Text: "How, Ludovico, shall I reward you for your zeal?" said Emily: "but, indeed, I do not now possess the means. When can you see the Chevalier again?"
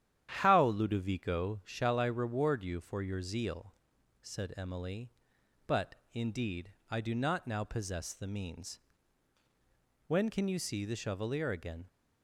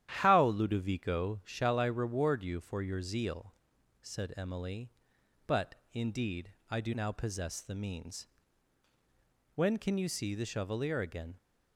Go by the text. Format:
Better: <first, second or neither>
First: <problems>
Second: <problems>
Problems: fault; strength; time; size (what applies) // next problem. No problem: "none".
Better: first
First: starts louder than the rest; strong; until 1.3 s; 10.5 dB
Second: starts louder than the rest; strong; until 1.1 s; 11 dB // skips "not"; at 6.9 s